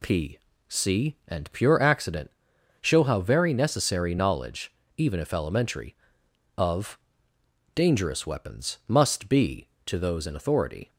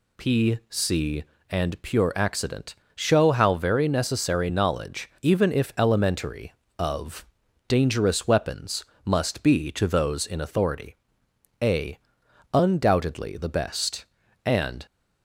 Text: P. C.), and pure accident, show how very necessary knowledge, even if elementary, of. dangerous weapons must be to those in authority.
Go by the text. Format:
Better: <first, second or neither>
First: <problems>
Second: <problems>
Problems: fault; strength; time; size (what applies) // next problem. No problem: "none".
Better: first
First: none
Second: pauses between "weapons" and "must"; slight; at 8.8 s; 0.18 s long // goes on to say "a Undoubtedly the best and"; strong; from 11.6 s on; 3.2 s long